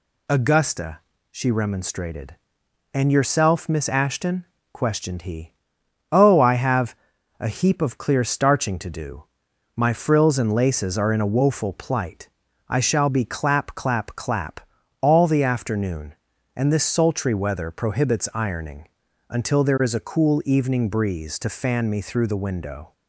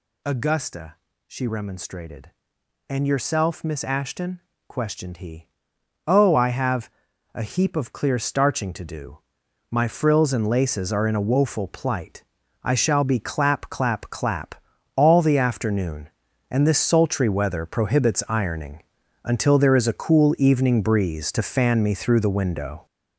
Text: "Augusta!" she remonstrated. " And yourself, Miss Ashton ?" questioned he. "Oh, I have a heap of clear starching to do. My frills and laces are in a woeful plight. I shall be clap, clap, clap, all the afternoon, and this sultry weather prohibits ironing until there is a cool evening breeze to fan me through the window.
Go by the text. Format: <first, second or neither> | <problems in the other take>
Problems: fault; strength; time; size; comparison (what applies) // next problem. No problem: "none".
first | gets louder; strong; throughout; 11.5 dB // pauses between "have" and "a"; at 6.8 s; 0.44 s long; also in the first // pauses between "ironing" and "until"; at 18.8 s; 0.42 s long; also in the first